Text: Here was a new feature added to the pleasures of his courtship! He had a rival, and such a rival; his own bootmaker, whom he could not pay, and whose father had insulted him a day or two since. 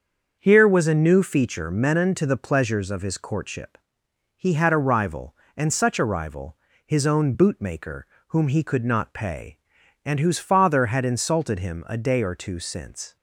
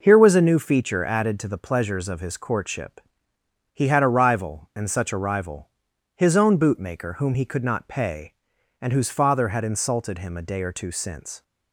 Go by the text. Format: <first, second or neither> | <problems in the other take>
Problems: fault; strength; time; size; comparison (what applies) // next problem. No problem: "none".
second | starts louder than the rest; until 1.4 s; 6.5 dB // says "menon" for "added"; at 1.6 s